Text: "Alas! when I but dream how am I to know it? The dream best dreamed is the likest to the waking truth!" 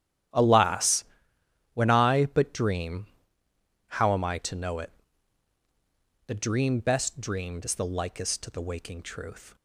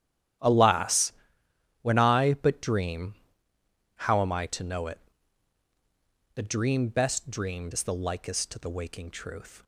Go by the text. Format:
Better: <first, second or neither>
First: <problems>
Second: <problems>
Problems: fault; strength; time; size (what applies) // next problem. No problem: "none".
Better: neither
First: starts louder than the rest; strong; until 2.0 s; 11.5 dB // pauses between "dream" and "how"; noticeable; at 3.0 s; 0.80 s long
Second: starts louder than the rest; strong; until 2.1 s; 11.5 dB // pauses between "dream" and "how"; noticeable; at 3.1 s; 0.80 s long